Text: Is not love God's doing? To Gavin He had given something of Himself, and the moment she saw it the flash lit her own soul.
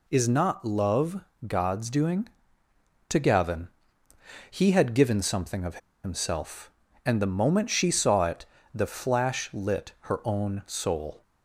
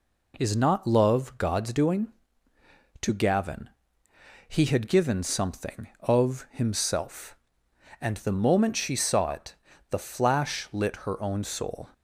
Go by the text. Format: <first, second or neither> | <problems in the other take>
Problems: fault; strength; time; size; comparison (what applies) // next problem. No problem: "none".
second | pauses between "love" and "God's"; slight; at 1.2 s; 0.28 s long // pauses between "Gavin" and "He"; noticeable; at 3.6 s; 0.86 s long; noticeable in the second // pauses between "of" and "Himself"; slight; at 5.7 s; 0.25 s long // pauses between "it" and "the"; slight; at 8.4 s; 0.26 s long; slight in the second